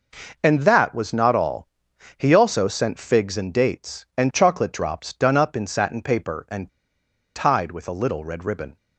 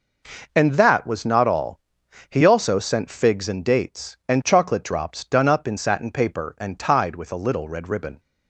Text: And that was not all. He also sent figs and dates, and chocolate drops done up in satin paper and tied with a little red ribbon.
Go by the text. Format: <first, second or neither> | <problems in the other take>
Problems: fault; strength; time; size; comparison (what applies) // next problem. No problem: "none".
second | pauses between "and" and "tied"; noticeable; at 6.7 s; 0.65 s long